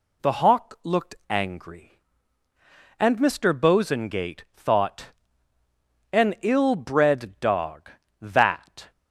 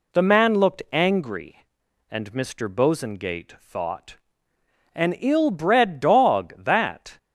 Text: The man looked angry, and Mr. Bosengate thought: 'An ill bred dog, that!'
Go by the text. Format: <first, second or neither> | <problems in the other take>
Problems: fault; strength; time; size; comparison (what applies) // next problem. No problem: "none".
second | says "hawk" for "man"; at 0.3 s // pauses between "looked" and "angry"; slight; at 1.1 s; 0.16 s long